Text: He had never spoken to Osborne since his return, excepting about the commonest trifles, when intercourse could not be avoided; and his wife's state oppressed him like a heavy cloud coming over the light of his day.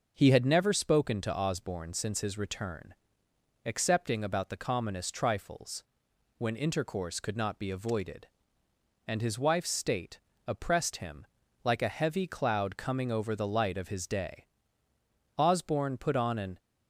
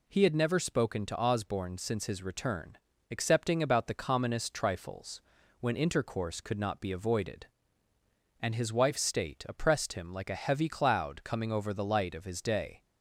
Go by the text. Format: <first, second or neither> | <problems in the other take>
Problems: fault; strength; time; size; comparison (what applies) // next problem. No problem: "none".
second | pauses between "state" and "oppressed"; slight; at 10.1 s; 0.28 s long // pauses between "him" and "like"; at 11.2 s; 0.40 s long // goes on to say "Osborne put on an"; noticeable; from 15.3 s on; 1.2 s long